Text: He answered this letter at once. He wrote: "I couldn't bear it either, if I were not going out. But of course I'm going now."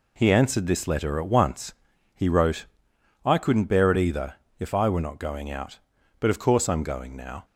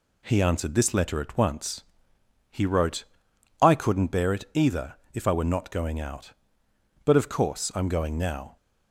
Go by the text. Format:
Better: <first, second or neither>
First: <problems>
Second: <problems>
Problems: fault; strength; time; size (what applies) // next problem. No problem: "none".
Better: neither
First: none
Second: none